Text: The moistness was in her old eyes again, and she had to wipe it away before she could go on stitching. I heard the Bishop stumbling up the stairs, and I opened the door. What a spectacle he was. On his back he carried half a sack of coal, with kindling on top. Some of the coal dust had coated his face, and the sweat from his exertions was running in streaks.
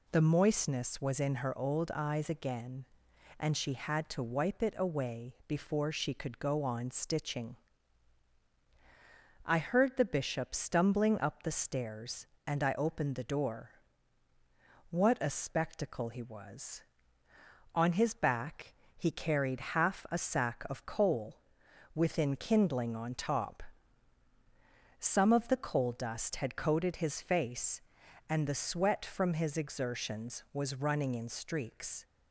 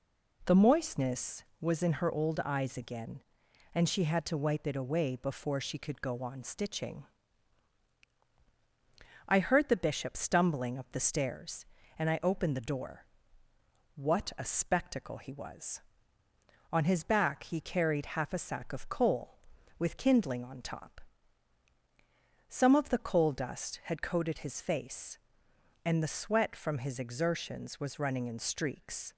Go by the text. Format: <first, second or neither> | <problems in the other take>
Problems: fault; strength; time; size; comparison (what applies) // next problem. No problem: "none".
second | pauses between "back" and "he"; slight; at 18.7 s; 0.24 s long // says "within" for "with"; at 21.9 s